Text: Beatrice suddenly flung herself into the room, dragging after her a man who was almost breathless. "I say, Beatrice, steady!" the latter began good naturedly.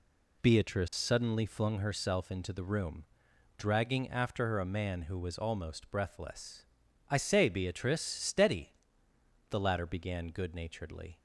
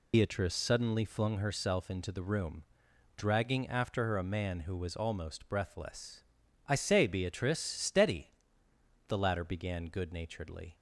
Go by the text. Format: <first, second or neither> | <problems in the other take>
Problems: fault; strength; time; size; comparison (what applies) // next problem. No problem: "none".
first | loses the start of "Beatrice"; at 0.1 s; 95 ms